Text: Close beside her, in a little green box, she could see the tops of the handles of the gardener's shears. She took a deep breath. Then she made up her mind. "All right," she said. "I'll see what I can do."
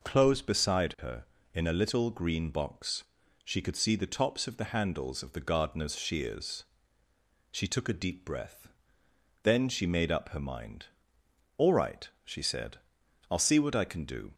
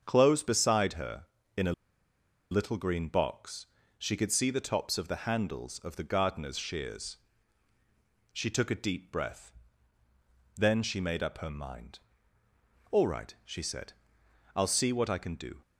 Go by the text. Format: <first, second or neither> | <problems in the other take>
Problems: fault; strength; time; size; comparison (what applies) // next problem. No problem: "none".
first | starts louder than the rest; strong; until 1.0 s; 7 dB // pauses between "a" and "little"; noticeable; at 1.7 s; 0.78 s long